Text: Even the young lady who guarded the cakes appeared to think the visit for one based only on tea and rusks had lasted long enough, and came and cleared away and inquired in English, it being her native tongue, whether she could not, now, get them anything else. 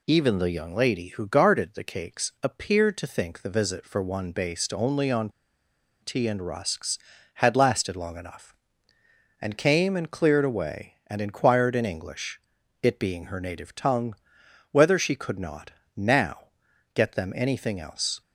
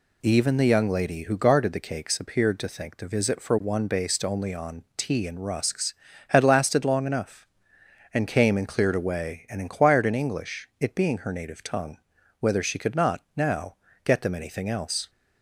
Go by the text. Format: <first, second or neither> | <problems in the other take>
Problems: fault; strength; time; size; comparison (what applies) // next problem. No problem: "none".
second | pauses between "on" and "tea"; noticeable; at 5.2 s; 0.72 s long